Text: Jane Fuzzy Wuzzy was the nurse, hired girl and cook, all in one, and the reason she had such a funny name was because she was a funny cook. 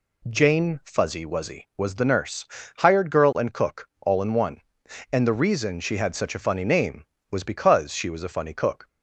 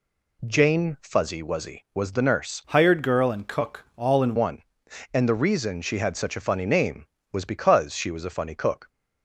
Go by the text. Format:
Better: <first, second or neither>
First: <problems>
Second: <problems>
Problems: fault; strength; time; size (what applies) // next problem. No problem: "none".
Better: first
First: none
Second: changes voice from "hired" to "in"; from 2.6 to 4.3 s; 1.7 s long